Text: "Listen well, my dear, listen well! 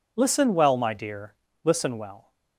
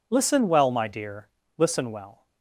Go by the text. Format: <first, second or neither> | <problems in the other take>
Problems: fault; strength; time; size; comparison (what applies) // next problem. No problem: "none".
neither | none